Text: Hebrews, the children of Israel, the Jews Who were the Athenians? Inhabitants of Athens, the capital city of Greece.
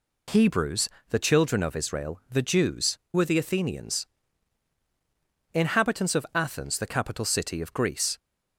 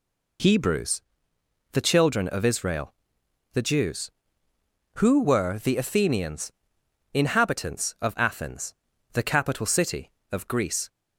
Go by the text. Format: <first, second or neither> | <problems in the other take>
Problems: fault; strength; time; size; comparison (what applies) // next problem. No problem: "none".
second | skips "Who"; at 3.0 s